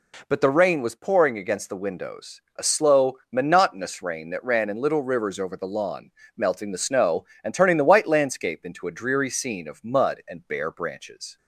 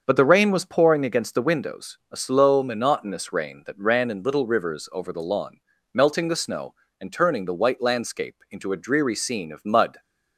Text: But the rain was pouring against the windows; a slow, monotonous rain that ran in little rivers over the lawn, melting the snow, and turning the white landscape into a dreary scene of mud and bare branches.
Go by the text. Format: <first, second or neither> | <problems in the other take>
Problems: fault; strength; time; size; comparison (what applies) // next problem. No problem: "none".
first | starts louder than the rest; until 1.0 s; 6.5 dB // stops before "and bare branches"; at 9.9 s